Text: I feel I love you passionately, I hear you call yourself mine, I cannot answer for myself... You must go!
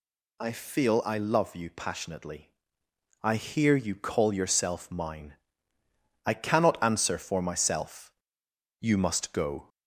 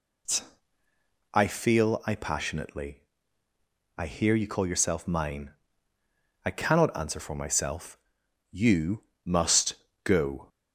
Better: first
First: none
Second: skips "love you"; at 2.1 s // pauses between "You" and "must"; slight; at 9.0 s; 0.24 s long // pauses between "must" and "go"; slight; at 9.7 s; 0.30 s long

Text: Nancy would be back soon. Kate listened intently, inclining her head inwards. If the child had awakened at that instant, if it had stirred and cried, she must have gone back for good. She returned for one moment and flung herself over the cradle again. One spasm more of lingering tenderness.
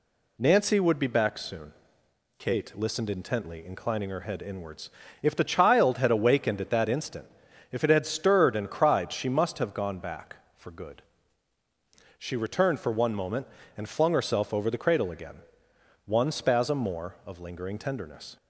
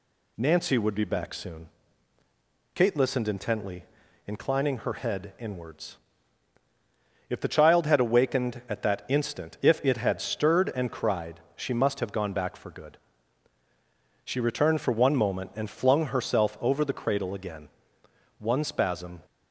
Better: first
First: none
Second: stops before "more of lingering tenderness"; at 19.2 s

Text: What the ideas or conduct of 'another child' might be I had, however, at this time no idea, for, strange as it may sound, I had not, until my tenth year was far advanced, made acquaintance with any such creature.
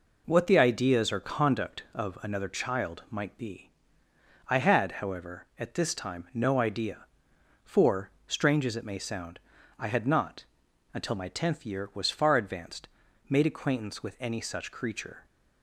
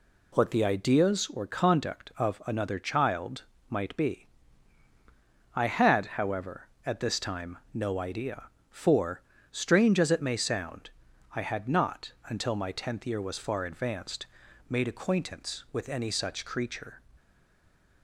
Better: first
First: pauses between "be" and "I"; noticeable; at 3.6 s; 0.78 s long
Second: pauses between "child" and "might"; slight; at 3.4 s; 0.26 s long // pauses between "be" and "I"; strong; at 4.2 s; 1.2 s long // stays silent after the last word; slight; from 17.1 s on; 0.9 s long

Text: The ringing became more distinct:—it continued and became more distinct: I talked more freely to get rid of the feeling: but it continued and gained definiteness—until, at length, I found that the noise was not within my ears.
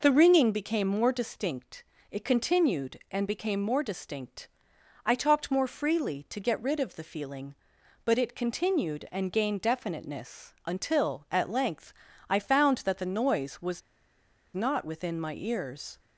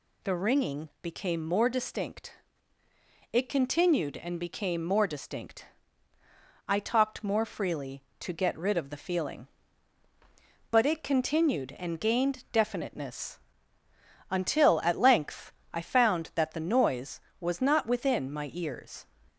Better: second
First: pauses between "was" and "not"; noticeable; at 13.7 s; 0.74 s long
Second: none

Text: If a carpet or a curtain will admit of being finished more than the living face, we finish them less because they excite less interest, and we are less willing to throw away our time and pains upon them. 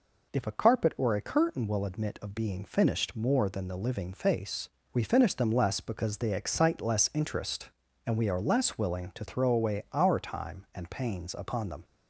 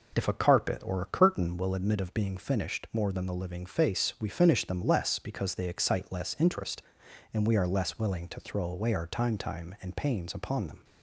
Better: first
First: none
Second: says "time" twice; at 9.3 s

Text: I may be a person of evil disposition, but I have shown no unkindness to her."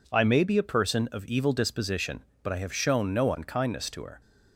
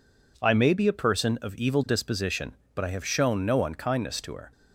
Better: neither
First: none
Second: none

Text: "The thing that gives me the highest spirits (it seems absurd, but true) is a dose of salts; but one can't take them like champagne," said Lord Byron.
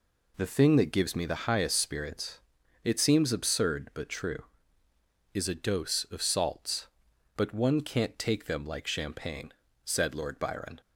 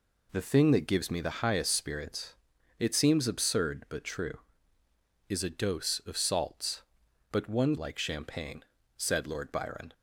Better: first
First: none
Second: skips "can't take them"; at 7.7 s

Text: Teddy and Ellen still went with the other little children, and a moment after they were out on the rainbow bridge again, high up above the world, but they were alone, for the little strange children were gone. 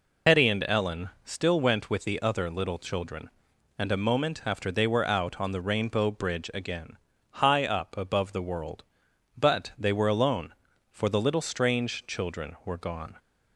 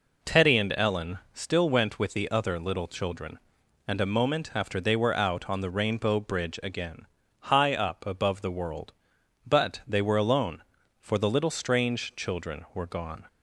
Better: second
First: loses the start of "Teddy"; at 0.2 s; 120 ms // pauses between "Ellen" and "still"; slight; at 1.0 s; 0.16 s long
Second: pauses between "Ellen" and "still"; slight; at 1.1 s; 0.16 s long

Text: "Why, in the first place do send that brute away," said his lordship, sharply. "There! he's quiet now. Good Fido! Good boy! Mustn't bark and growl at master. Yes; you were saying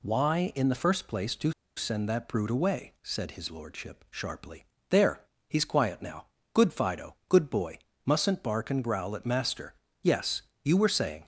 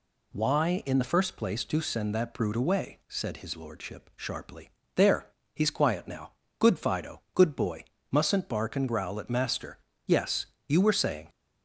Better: second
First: pauses between "do" and "send"; slight; at 1.5 s; 0.24 s long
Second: none

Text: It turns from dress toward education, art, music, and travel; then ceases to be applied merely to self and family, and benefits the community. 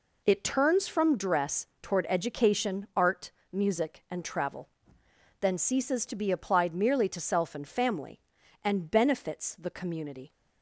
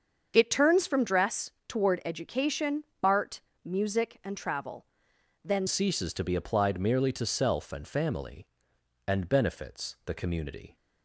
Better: first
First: pauses between "dress" and "toward"; slight; at 1.6 s; 0.15 s long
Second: starts louder than the rest; strong; until 1.3 s; 7 dB // pauses between "dress" and "toward"; slight; at 1.5 s; 0.18 s long // changes voice at "ceases"; from 5.6 s on; 5.1 s long

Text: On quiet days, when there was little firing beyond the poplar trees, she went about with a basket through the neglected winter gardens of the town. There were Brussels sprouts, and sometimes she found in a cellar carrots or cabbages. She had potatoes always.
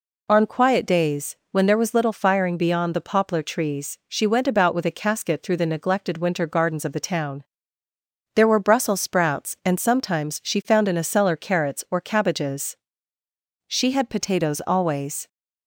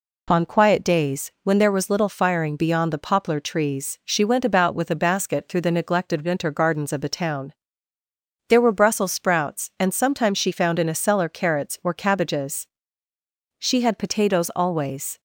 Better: second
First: says "casket" for "basket"; at 4.9 s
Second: none

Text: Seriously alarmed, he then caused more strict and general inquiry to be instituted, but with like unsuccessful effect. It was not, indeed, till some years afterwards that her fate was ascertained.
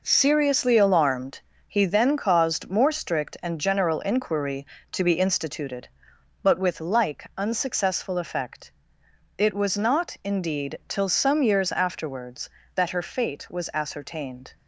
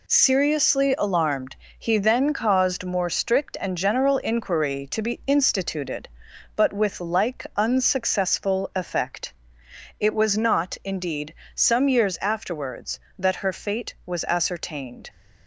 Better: first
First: none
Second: skips "till"; at 11.4 s

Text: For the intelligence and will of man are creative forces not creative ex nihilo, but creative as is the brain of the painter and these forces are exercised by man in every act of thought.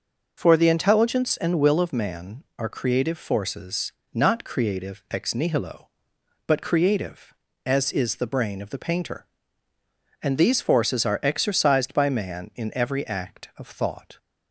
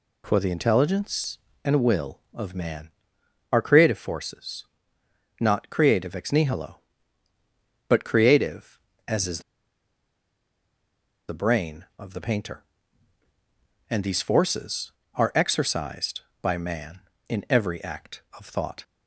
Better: first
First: pauses between "forces" and "not"; slight; at 3.9 s; 0.24 s long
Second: pauses between "forces" and "not"; noticeable; at 4.6 s; 0.74 s long // pauses between "is" and "the"; strong; at 9.4 s; 1.8 s long

